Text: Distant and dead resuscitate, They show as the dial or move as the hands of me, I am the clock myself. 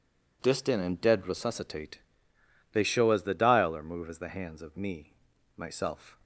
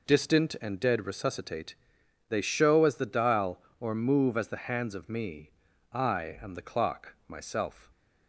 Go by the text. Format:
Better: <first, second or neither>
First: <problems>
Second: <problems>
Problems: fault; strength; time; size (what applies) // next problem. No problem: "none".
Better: second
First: skips "I am the clock"; at 5.3 s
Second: none